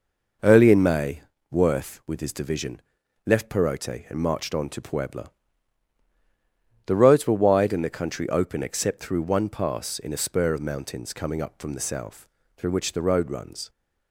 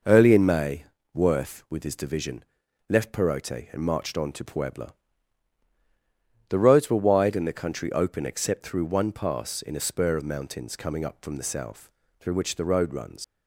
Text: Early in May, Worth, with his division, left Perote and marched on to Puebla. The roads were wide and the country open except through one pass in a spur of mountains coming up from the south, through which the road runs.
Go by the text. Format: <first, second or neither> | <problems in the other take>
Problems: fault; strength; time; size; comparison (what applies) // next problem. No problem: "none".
first | leaves "runs" unfinished; at 13.2 s; 80 ms